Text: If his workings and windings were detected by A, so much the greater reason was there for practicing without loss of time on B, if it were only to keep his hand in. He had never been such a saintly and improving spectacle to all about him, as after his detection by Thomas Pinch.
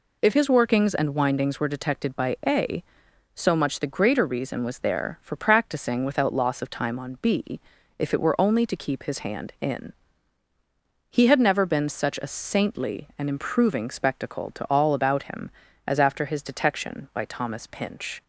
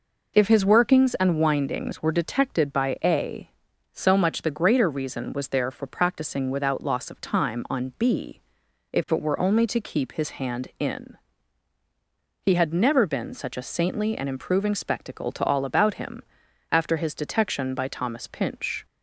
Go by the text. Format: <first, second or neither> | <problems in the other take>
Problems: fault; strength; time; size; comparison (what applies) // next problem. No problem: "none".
first | skips "as"; at 16.4 s